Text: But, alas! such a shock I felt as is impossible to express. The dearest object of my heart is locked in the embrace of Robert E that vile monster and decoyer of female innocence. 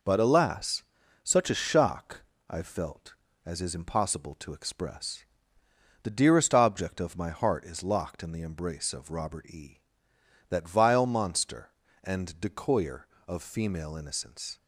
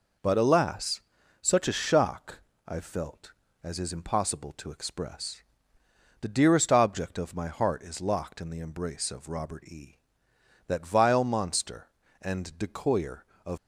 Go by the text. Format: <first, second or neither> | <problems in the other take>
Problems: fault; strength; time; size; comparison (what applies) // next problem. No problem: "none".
first | pauses between "shock" and "I"; slight; at 2.4 s; 0.26 s long; slight in the first // stops before "female innocence"; at 13.5 s